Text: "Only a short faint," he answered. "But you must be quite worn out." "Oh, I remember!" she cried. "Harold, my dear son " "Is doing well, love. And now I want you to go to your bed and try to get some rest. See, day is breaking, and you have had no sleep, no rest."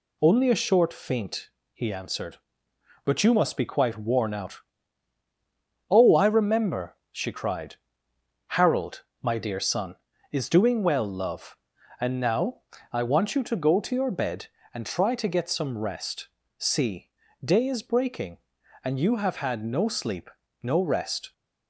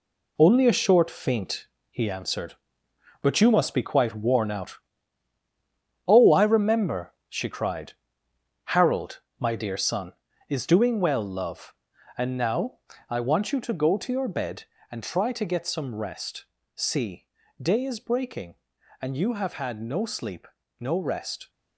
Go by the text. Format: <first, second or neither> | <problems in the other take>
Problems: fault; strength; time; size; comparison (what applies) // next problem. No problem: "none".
first | gets quieter; strong; throughout; 7.5 dB // pauses between "now" and "I"; slight; at 12.7 s; 0.30 s long; slight in the first